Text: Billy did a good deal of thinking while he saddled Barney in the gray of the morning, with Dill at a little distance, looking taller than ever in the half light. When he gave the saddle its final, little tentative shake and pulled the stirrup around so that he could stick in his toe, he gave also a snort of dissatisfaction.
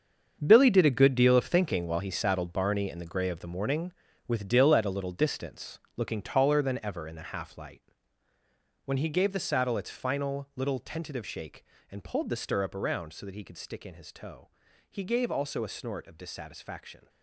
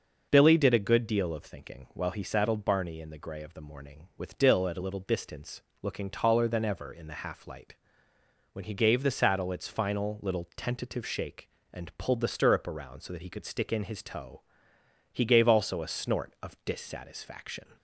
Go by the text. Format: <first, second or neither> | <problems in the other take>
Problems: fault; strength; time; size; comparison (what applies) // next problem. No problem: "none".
second | gets quieter; strong; throughout; 12.5 dB